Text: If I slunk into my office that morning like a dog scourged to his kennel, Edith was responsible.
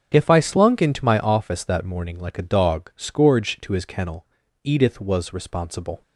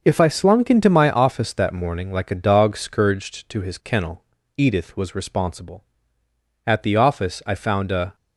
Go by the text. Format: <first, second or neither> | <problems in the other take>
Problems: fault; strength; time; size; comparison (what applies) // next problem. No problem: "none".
first | starts louder than the rest; until 1.0 s; 6.5 dB; strong in the first // goes on to say "At the office I found a"; from 6.6 s on; 1.4 s long